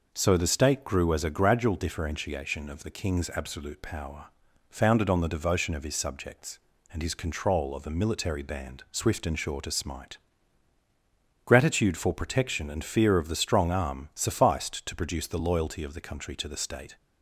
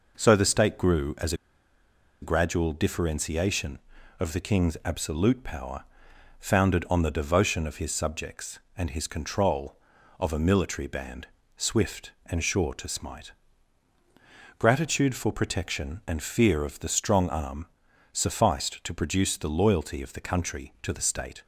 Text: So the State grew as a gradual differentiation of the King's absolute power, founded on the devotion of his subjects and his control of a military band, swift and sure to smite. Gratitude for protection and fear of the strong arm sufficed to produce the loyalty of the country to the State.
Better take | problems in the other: first | pauses between "as" and "a"; noticeable; at 1.3 s; 0.88 s long // pauses between "arm" and "sufficed"; noticeable; at 17.6 s; 0.48 s long

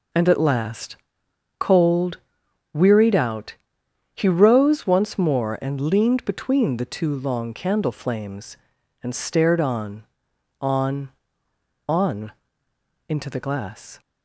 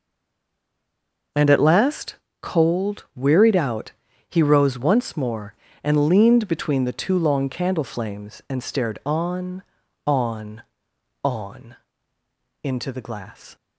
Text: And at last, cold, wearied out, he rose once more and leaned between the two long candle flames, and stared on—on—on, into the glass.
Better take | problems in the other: first | stays silent before the first word; noticeable; until 1.3 s; 1.3 s long

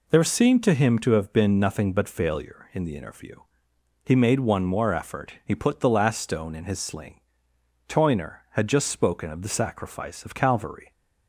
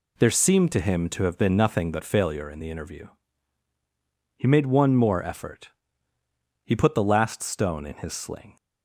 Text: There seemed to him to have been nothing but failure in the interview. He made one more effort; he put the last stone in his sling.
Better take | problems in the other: second | goes on to say "Toyner had just spoken of the sacrifice of Calvary"; strong; from 7.8 s on; 3.0 s long

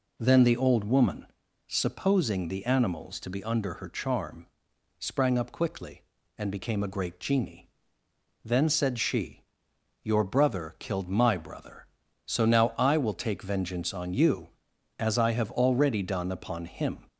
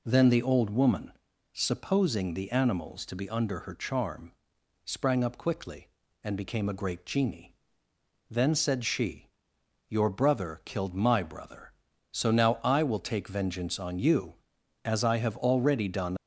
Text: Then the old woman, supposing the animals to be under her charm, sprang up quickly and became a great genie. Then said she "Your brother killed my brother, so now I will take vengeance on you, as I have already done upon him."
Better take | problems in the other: first | pauses between "she" and "Your"; noticeable; at 9.2 s; 0.60 s long; noticeable in the first // stops before "upon him"; at 16.1 s

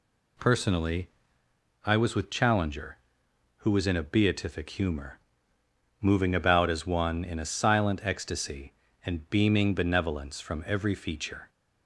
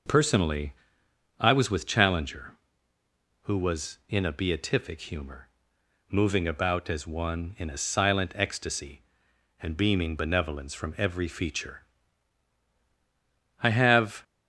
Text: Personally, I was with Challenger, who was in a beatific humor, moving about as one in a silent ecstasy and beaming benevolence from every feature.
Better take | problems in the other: first | goes on to say "I have"; noticeable; from 13.6 s on; 0.62 s long

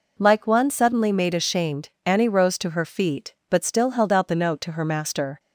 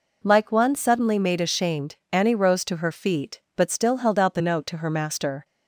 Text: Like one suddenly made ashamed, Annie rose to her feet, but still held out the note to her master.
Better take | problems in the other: neither | none

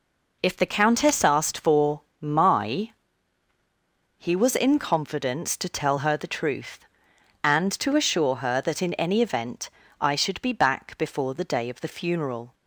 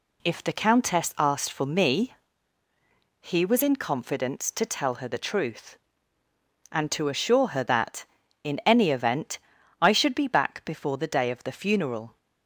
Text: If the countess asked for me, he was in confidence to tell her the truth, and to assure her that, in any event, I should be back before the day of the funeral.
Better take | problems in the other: second | says "my" for "me"; at 2.2 s

